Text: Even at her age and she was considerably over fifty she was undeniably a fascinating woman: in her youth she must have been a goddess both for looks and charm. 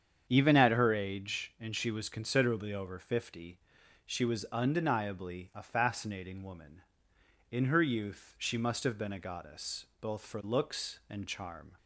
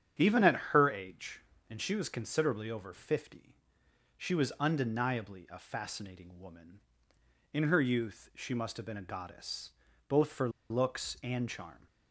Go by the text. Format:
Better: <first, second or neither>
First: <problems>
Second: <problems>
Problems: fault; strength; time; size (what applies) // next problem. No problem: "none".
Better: first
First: starts louder than the rest; strong; until 1.3 s; 8 dB // pauses between "fifty" and "she"; noticeable; at 3.5 s; 0.46 s long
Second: starts louder than the rest; strong; until 1.3 s; 8.5 dB // pauses between "at" and "her"; slight; at 0.5 s; 0.16 s long // pauses between "fifty" and "she"; noticeable; at 3.5 s; 0.64 s long // pauses between "goddess" and "both"; at 9.6 s; 0.38 s long // pauses between "for" and "looks"; slight; at 10.4 s; 0.20 s long